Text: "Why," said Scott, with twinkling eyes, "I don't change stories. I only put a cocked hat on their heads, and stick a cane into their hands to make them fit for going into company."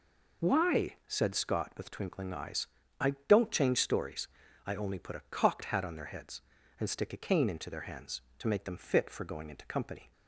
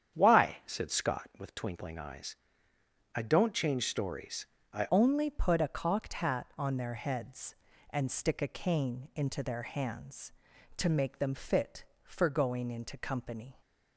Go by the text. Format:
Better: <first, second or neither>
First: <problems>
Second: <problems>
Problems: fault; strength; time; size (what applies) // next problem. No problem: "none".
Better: first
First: none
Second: starts louder than the rest; strong; until 1.1 s; 9 dB // changes voice at "only"; from 4.9 s on; 8.7 s long